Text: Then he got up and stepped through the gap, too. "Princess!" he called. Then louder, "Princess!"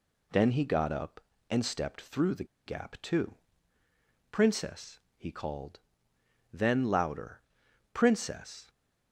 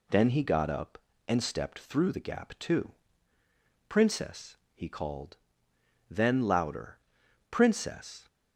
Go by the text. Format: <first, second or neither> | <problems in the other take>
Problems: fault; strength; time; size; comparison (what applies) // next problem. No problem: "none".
second | pauses between "the" and "gap"; slight; at 2.4 s; 0.20 s long